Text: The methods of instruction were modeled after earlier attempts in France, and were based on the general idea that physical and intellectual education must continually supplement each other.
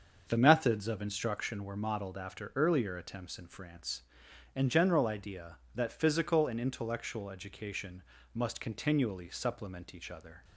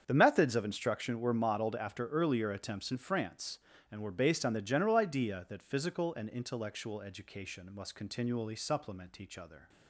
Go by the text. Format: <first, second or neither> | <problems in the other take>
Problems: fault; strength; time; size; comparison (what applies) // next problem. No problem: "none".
second | starts louder than the rest; until 1.2 s; 6.5 dB; strong in the second // skips "were based on the"; at 4.6 s // pauses between "education" and "must"; slight; at 8.0 s; 0.32 s long